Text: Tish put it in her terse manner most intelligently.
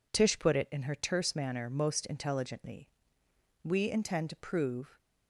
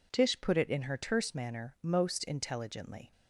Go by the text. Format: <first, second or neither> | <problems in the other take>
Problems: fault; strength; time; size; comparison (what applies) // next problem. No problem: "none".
second | goes on to say "We intend to prove"; from 3.6 s on; 1.3 s long